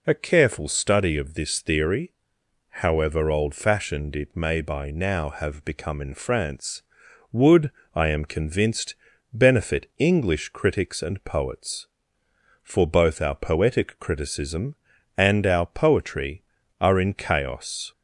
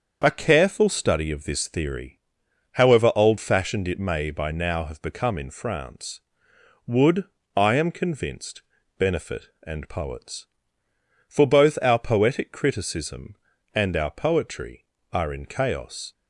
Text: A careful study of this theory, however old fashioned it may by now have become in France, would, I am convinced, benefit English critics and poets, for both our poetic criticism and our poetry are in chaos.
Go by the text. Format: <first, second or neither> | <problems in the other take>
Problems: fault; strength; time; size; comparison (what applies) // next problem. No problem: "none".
first | starts louder than the rest; until 1.2 s; 7 dB // skips "English critics"; at 9.5 s